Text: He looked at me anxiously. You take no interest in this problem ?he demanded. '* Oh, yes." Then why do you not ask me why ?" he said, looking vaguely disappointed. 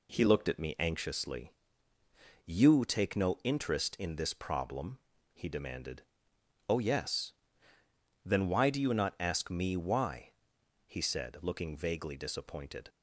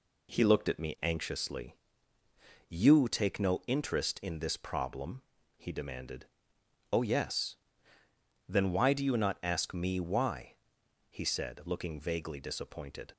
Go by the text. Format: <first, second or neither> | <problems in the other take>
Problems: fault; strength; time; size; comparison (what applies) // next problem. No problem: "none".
neither | none